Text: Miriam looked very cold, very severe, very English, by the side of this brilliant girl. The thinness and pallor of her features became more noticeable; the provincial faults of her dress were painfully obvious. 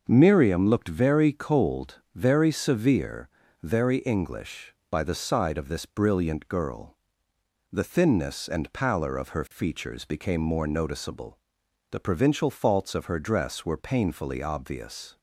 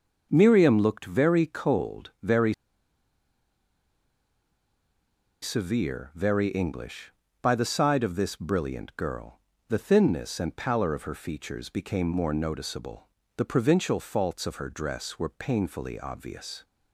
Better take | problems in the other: first | starts louder than the rest; until 1.3 s; 6.5 dB; noticeable in the first // pauses between "very" and "severe"; strong; at 2.5 s; 2.8 s long

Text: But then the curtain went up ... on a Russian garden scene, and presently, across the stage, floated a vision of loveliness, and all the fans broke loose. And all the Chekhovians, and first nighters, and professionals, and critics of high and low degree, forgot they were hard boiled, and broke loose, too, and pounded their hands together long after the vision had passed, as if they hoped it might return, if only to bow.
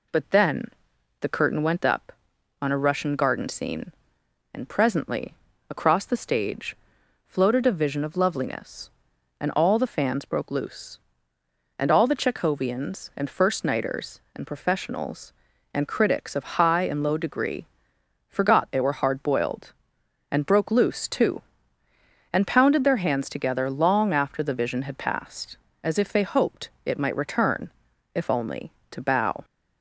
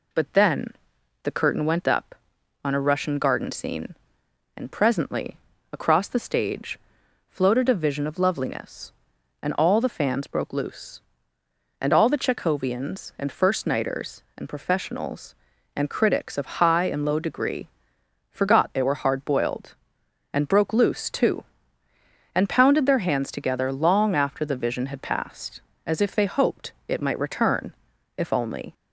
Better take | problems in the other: first | pauses between "then" and "the"; noticeable; at 0.6 s; 0.56 s long; noticeable in the first // stops before "to bow"; at 28.7 s

